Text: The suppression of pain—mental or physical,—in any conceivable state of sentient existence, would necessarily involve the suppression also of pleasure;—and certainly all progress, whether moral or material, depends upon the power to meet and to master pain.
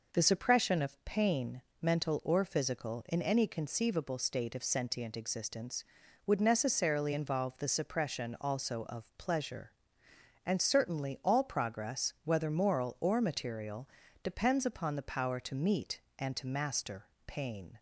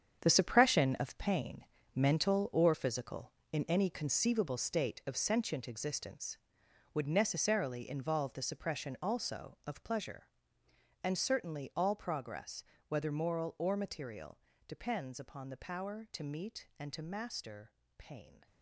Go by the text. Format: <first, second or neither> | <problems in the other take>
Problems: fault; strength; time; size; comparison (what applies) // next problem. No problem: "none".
first | gets quieter; strong; throughout; 11 dB // pauses between "master" and "pain"; slight; at 17.7 s; 0.26 s long; slight in the first